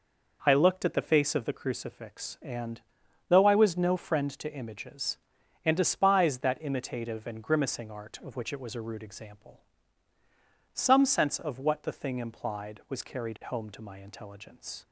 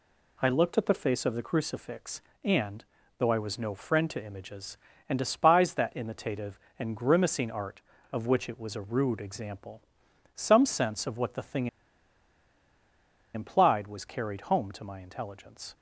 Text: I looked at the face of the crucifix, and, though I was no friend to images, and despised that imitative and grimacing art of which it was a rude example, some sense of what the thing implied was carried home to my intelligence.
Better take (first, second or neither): first